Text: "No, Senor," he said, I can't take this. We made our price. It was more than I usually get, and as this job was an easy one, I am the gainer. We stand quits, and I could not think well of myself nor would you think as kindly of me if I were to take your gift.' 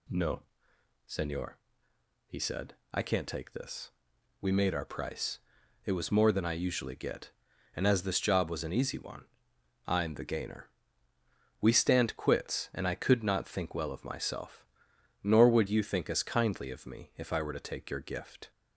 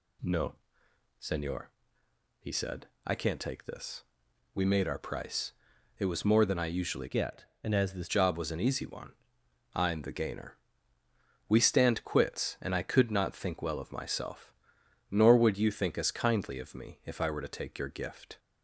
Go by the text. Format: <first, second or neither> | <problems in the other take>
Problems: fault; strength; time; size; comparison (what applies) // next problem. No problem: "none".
first | changes voice from "get" to "this"; from 7.0 to 8.0 s; 1.0 s long // pauses between "myself" and "nor"; noticeable; at 14.5 s; 0.60 s long; noticeable in the first